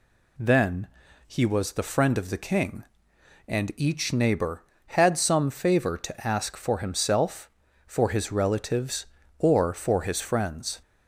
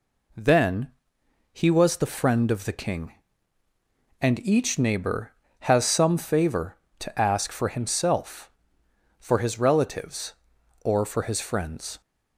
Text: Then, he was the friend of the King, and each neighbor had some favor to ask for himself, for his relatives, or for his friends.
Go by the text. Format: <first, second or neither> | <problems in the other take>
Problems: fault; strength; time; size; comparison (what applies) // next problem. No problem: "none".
first | says "has" for "had"; at 5.6 s